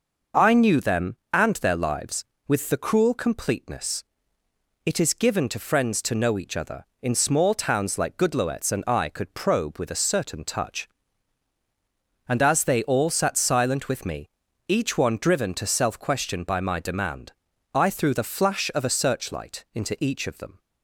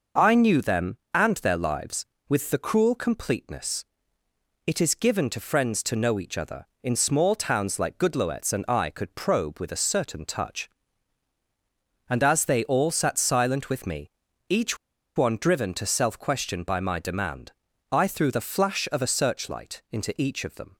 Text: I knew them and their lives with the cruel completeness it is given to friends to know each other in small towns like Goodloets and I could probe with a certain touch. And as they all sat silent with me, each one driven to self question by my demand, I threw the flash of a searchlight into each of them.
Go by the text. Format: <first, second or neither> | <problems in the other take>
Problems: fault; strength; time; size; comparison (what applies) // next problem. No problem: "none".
first | pauses between "completeness" and "it"; noticeable; at 3.8 s; 0.80 s long; noticeable in the first // pauses between "each" and "one"; at 14.7 s; 0.39 s long